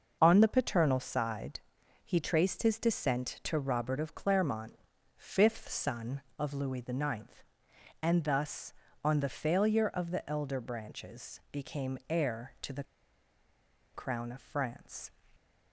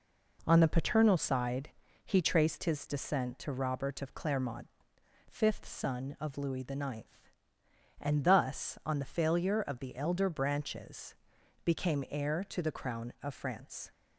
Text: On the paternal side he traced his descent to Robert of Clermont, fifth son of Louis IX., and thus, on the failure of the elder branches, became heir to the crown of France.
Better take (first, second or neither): second